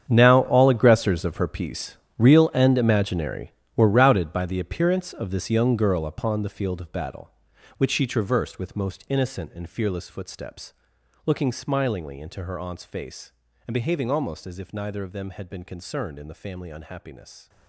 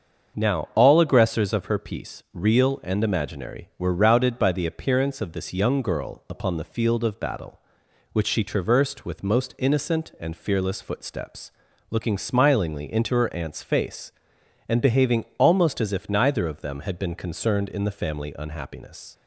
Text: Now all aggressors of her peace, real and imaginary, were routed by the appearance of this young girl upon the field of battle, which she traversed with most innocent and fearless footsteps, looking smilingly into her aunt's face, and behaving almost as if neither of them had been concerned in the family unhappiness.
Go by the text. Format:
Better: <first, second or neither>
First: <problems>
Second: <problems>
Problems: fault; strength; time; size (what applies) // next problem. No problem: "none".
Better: second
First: gets quieter; strong; throughout; 15.5 dB // starts louder than the rest; strong; until 1.0 s; 8.5 dB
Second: starts louder than the rest; until 1.4 s; 6.5 dB